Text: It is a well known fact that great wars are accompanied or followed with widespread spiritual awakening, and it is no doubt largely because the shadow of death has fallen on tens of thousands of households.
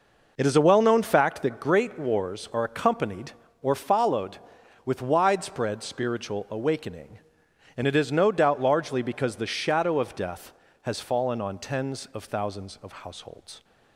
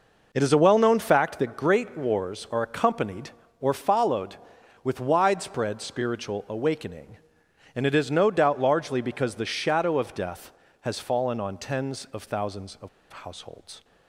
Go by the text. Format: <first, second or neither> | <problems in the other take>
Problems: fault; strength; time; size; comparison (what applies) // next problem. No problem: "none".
first | pauses between "of" and "households"; slight; at 12.8 s; 0.23 s long